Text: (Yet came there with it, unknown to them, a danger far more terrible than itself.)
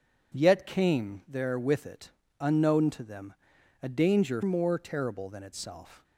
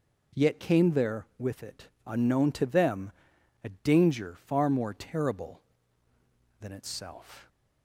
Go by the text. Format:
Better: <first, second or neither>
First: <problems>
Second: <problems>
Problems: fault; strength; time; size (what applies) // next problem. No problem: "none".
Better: second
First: skips "far"; at 4.4 s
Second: none